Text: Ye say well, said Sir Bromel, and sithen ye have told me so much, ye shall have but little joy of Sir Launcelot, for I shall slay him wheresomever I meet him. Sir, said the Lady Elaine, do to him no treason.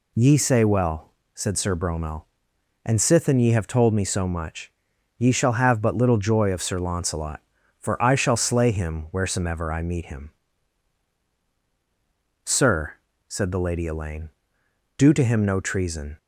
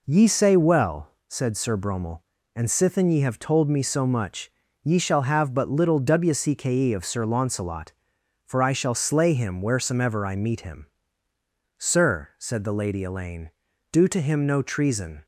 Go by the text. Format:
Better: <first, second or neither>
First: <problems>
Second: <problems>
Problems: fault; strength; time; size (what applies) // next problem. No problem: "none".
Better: first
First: none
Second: says "wcke" for "joy"; at 5.9 s